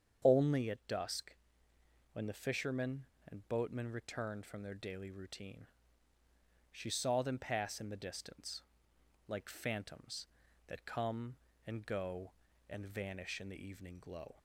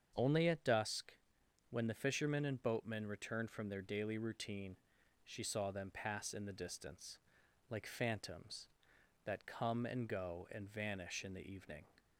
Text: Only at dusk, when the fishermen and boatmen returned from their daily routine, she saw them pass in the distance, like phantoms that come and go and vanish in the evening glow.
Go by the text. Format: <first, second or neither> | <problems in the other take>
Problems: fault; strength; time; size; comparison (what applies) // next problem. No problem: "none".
first | starts louder than the rest; strong; until 1.1 s; 7.5 dB; strong in the first // stops before "glow"; at 11.9 s